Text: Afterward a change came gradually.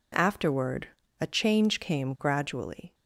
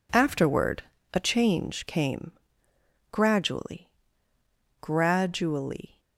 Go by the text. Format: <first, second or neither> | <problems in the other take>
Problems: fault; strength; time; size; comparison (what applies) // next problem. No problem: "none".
first | pauses between "Afterward" and "a"; slight; at 0.8 s; 0.30 s long; slight in the first // pauses between "came" and "gradually"; noticeable; at 2.3 s; 0.80 s long // says "gradually" twice; at 4.7 s